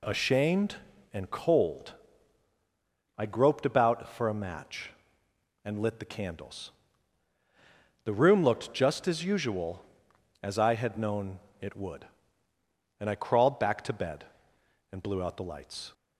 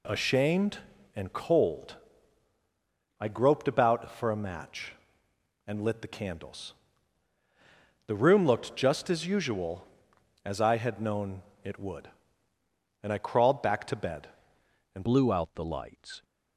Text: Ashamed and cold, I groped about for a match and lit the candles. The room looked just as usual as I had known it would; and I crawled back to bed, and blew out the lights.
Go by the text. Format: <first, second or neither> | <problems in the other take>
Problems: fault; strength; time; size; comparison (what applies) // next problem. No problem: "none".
first | pauses between "known" and "it"; slight; at 11.4 s; 0.22 s long; slight in the first // changes voice at "blew"; from 15.0 s on; 1.2 s long